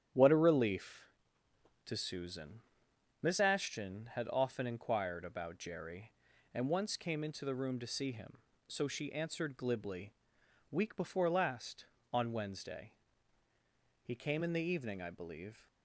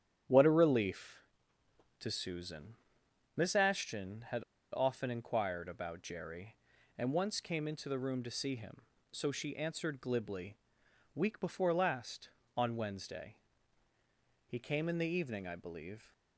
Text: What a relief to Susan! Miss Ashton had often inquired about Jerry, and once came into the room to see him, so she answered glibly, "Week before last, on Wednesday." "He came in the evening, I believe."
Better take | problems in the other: first | starts louder than the rest; strong; until 2.0 s; 9.5 dB; strong in the first // pauses between "had" and "often"; slight; at 4.4 s; 0.32 s long

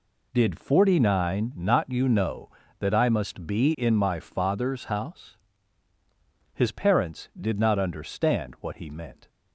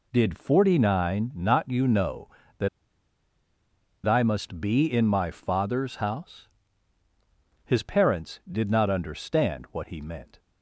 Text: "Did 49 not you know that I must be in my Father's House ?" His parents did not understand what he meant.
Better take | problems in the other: first | pauses between "that" and "I"; strong; at 2.6 s; 1.3 s long

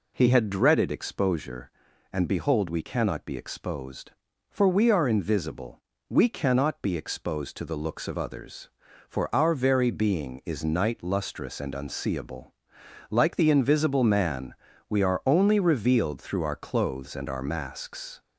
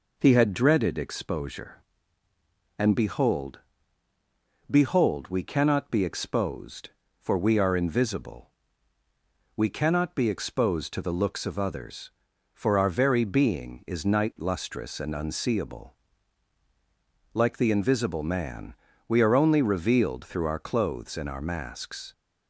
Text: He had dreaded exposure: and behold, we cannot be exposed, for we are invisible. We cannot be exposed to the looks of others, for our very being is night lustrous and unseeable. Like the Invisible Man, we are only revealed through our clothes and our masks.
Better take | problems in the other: first | says "behold" twice; at 4.6 s

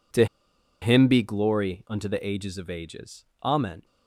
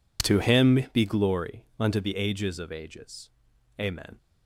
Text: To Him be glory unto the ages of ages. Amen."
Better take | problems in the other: second | pauses between "To" and "Him"; noticeable; at 0.2 s; 0.56 s long

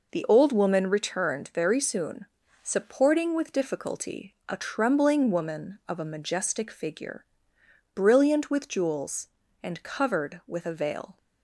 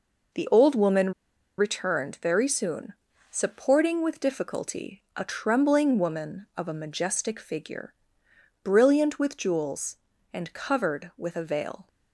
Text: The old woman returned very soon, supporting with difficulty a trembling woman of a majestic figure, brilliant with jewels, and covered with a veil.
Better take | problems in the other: first | pauses between "woman" and "returned"; at 1.1 s; 0.45 s long

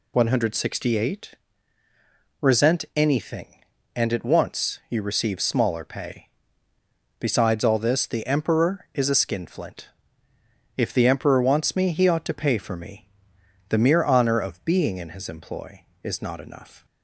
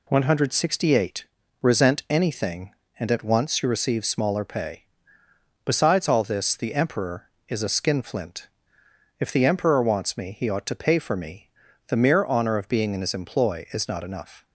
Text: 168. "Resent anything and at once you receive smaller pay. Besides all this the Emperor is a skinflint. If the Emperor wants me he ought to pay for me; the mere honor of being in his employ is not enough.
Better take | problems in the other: neither | none

